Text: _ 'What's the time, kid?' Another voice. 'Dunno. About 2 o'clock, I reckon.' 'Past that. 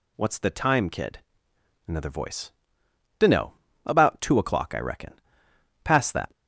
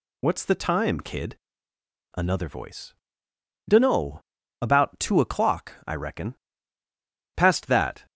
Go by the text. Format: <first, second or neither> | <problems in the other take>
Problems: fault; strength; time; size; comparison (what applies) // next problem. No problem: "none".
neither | none